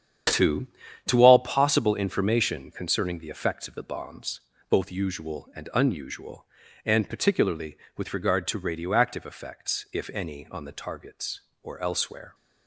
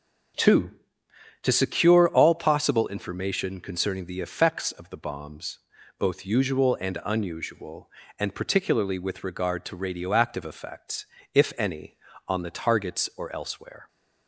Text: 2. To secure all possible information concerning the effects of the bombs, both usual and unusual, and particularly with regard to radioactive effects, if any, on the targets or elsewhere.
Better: second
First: starts louder than the rest; strong; until 1.6 s; 9 dB // skips "secure"; at 1.2 s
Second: starts louder than the rest; until 2.0 s; 6.5 dB

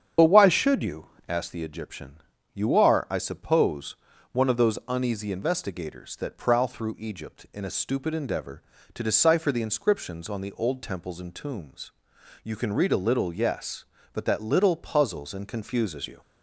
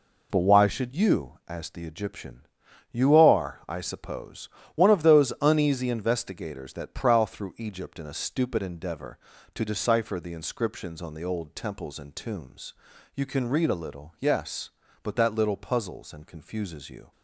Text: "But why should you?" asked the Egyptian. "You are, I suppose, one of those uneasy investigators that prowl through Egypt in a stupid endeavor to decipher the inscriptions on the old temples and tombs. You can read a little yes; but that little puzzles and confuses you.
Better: second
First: loses the start of "But"; at 0.1 s; 40 ms // starts louder than the rest; strong; until 1.4 s; 8.5 dB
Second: none

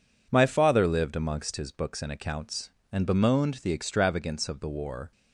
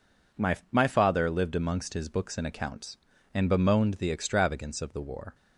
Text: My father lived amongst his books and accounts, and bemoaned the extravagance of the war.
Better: first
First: none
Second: says "My" twice; at 0.7 s

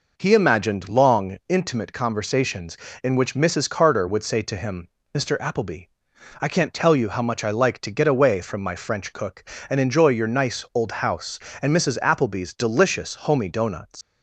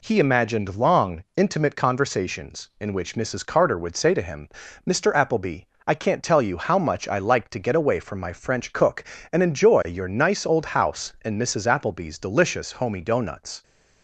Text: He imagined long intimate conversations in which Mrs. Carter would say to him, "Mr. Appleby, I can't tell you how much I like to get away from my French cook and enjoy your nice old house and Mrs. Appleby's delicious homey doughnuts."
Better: second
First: leaves "doughnuts" unfinished; at 14.0 s; 125 ms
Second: none

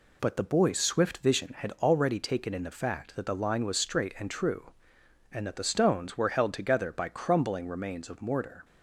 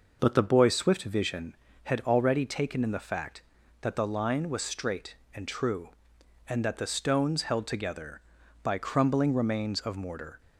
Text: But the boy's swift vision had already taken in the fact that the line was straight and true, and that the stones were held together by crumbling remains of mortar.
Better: first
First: none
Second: skips "were"; at 7.4 s

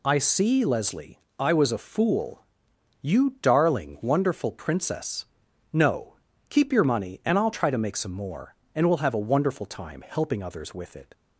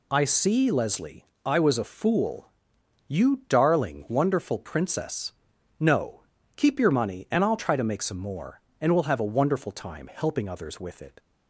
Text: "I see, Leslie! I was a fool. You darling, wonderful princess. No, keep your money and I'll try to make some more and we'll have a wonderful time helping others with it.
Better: neither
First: none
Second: none

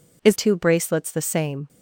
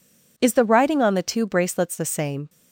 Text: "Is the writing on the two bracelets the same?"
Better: second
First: skips "the writing on the"; at 0.3 s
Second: none

